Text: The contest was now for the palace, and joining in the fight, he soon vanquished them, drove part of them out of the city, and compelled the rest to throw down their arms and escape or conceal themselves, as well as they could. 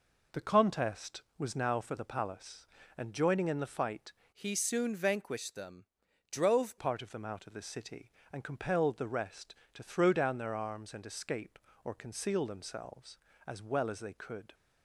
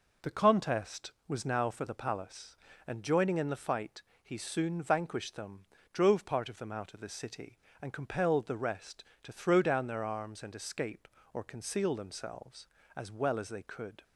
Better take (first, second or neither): second